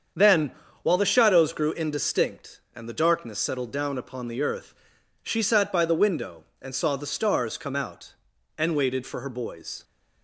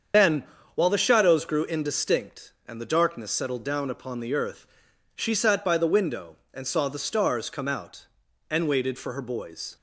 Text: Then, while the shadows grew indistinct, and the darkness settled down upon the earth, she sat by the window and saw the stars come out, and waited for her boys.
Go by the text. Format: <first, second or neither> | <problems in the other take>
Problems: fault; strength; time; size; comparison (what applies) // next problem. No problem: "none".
first | loses the start of "Then"; at 0.1 s; 65 ms // starts louder than the rest; strong; until 1.4 s; 7.5 dB; strong in the first